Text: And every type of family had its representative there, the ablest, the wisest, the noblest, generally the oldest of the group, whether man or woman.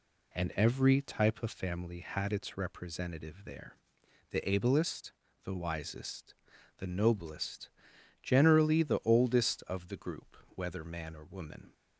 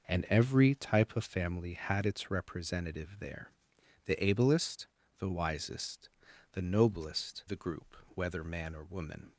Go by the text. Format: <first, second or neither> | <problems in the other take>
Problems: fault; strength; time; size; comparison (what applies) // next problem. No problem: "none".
first | skips "generally the oldest of"; at 7.4 s